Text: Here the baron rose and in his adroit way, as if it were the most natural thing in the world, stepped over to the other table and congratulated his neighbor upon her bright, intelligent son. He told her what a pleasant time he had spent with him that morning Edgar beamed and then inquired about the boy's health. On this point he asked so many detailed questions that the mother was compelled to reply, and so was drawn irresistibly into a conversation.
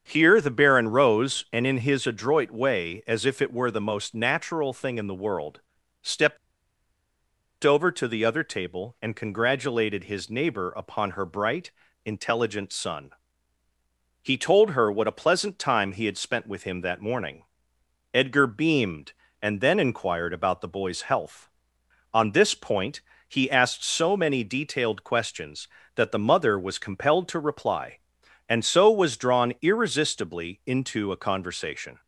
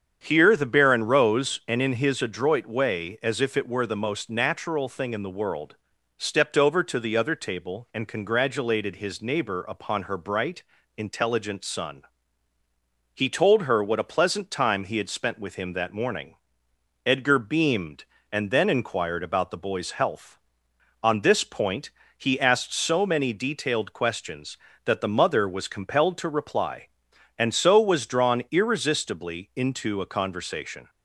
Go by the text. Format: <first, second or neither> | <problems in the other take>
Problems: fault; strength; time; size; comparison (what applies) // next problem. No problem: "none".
second | starts louder than the rest; strong; until 1.0 s; 7.5 dB; strong in the second // pauses between "stepped" and "over"; strong; at 6.3 s; 1.2 s long // pauses between "morning" and "Edgar"; noticeable; at 17.4 s; 0.68 s long; noticeable in the second // pauses between "point" and "he"; slight; at 23.0 s; 0.26 s long; slight in the second